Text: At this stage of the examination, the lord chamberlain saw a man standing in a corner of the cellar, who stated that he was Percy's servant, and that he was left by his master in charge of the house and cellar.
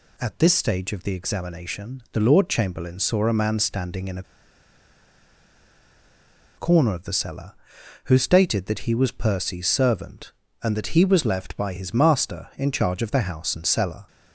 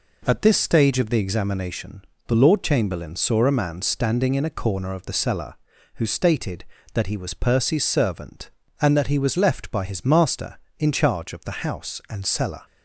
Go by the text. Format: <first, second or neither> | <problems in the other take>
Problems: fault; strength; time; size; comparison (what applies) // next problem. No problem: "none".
second | pauses between "a" and "corner"; strong; at 4.2 s; 2.3 s long